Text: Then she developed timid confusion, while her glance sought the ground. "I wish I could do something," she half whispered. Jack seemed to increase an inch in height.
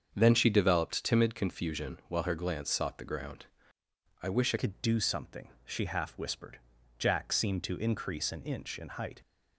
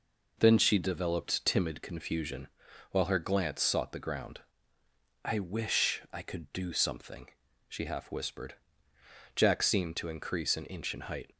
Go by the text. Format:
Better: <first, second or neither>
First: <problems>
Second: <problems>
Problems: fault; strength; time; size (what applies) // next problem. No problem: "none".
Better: second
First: starts louder than the rest; strong; until 1.1 s; 7 dB // changes voice at "could"; from 4.5 s on; 4.7 s long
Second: none